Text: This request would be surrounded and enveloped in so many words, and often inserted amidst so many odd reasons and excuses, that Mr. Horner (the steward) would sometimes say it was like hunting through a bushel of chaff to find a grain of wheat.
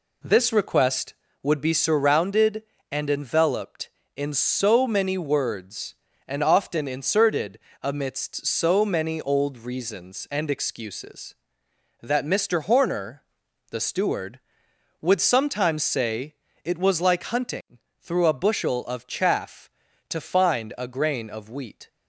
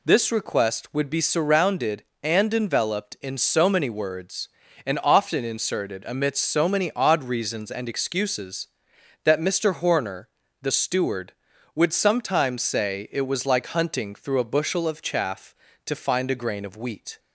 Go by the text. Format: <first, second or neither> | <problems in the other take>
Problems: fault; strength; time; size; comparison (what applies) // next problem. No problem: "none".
second | pauses between "inserted" and "amidst"; slight; at 7.5 s; 0.24 s long // says "old" for "odd"; at 9.2 s // pauses between "say" and "it"; slight; at 16.3 s; 0.28 s long // pauses between "hunting" and "through"; slight; at 17.7 s; 0.20 s long